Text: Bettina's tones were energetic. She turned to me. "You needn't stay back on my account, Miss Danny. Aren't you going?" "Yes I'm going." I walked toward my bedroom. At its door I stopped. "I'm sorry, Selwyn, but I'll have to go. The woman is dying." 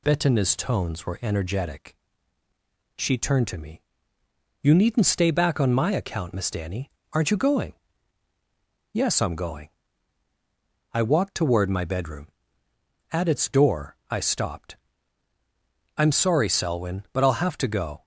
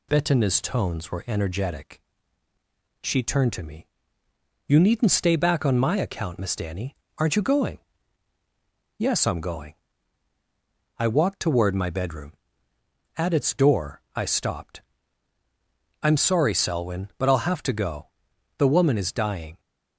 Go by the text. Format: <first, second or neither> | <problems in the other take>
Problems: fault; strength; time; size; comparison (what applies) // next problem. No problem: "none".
second | stops before "The woman is dying"; at 18.0 s